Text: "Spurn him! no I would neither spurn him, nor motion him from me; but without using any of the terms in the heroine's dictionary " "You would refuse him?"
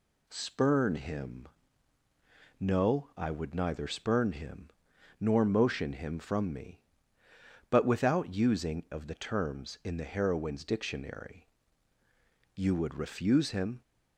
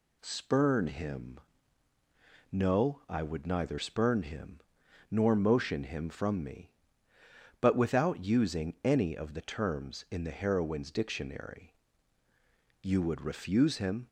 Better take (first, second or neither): second